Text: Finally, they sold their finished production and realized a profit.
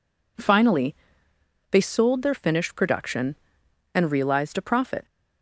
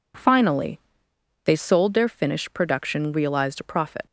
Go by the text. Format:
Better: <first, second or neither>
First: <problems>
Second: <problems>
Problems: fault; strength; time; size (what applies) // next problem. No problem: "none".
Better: first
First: none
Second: skips "and"; at 3.1 s